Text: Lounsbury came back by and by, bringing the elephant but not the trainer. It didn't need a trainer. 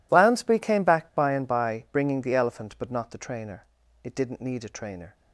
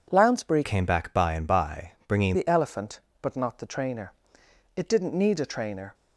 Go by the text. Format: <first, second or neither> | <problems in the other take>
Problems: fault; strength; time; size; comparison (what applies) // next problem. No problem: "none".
first | changes voice from "came" to "bringing"; from 0.6 to 2.3 s; 1.7 s long